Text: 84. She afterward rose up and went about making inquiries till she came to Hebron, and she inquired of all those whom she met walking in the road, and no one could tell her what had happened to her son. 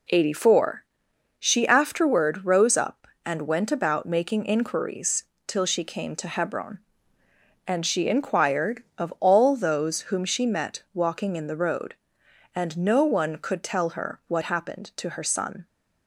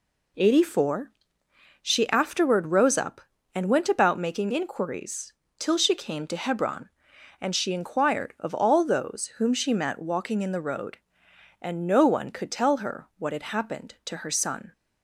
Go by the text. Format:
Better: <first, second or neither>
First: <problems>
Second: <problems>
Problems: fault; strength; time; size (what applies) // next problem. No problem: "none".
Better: second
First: pauses between "inquiries" and "till"; slight; at 5.2 s; 0.24 s long // skips "had"; at 14.4 s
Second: pauses between "inquiries" and "till"; slight; at 5.3 s; 0.26 s long